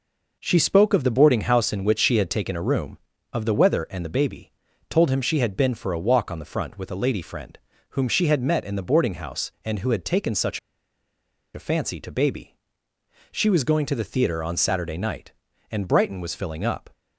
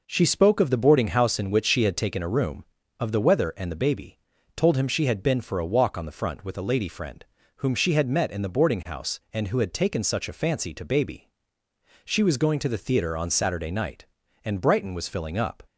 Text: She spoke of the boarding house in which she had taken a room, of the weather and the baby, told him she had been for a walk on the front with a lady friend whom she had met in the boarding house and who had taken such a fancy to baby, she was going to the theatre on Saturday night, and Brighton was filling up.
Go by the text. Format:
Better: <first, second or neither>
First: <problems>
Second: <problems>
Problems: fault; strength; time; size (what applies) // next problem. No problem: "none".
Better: second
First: pauses between "friend" and "whom"; slight; at 7.5 s; 0.34 s long // pauses between "such" and "a"; noticeable; at 10.5 s; 0.96 s long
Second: pauses between "friend" and "whom"; slight; at 7.2 s; 0.34 s long